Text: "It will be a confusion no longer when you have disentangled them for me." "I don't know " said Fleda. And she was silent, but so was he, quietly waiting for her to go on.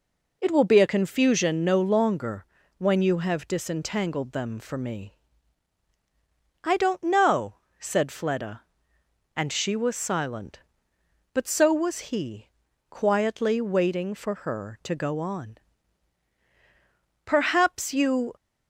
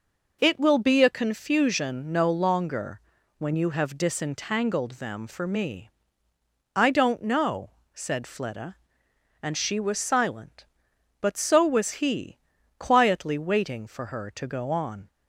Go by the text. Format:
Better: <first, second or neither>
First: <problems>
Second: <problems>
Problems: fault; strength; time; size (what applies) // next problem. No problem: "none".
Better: second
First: pauses between "longer" and "when"; slight; at 2.4 s; 0.32 s long // goes on to say "Perhaps you"; noticeable; from 17.2 s on; 1.1 s long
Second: pauses between "longer" and "when"; at 3.0 s; 0.38 s long